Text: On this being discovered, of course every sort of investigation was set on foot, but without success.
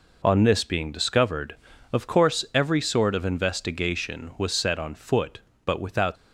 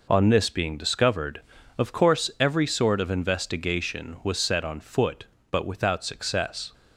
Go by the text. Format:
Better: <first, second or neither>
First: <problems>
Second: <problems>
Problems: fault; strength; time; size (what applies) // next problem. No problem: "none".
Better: second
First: stops before "success"; at 6.1 s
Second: none